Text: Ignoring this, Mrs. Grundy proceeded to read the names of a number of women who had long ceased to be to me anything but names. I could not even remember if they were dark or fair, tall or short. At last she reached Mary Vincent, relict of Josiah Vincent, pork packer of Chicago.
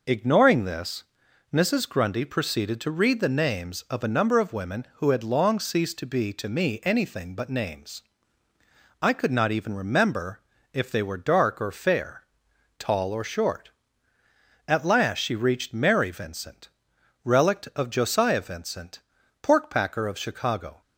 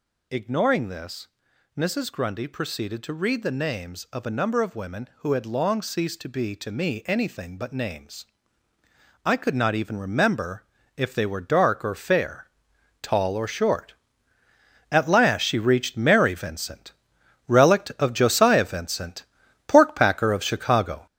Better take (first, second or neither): first